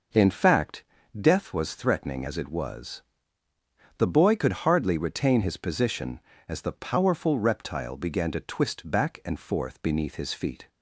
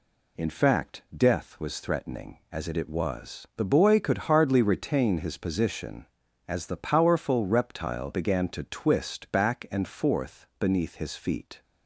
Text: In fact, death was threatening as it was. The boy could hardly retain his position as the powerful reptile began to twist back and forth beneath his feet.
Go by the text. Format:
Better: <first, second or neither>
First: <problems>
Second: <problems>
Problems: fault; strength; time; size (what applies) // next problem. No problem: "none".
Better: first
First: none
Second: says "it" twice; at 2.7 s